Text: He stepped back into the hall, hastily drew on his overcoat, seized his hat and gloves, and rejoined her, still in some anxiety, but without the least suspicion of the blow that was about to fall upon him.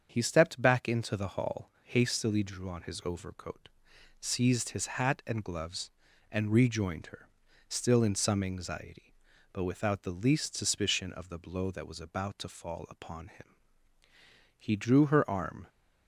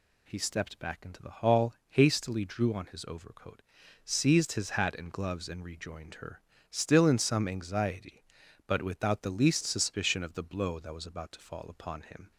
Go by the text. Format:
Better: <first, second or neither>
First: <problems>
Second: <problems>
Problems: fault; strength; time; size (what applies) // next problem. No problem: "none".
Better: second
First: starts louder than the rest; strong; until 1.1 s; 7.5 dB // goes on to say "He drew her arm"; noticeable; from 14.5 s on; 1.1 s long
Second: none